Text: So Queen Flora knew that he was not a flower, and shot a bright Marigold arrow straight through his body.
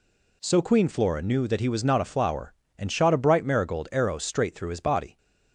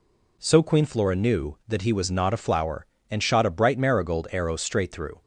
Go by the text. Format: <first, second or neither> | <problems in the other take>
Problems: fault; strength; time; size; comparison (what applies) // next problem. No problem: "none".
first | stops before "his body"; at 5.2 s